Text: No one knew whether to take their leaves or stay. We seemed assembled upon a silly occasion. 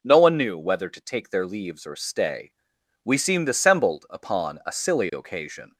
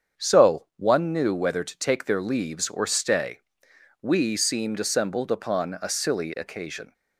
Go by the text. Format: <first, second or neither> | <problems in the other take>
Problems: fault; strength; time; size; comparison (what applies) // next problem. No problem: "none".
first | starts louder than the rest; strong; until 1.3 s; 7.5 dB // says "So" for "No"; at 0.1 s